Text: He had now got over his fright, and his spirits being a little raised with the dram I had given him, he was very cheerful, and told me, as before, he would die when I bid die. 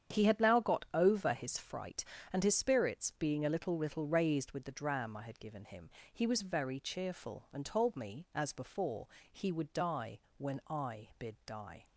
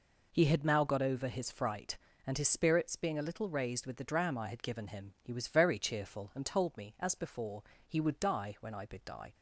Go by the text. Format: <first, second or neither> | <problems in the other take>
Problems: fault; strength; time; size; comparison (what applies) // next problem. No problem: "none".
second | starts louder than the rest; strong; until 1.2 s; 8.5 dB // says "little" twice; at 3.7 s // pauses between "die" and "when"; slight; at 10.1 s; 0.18 s long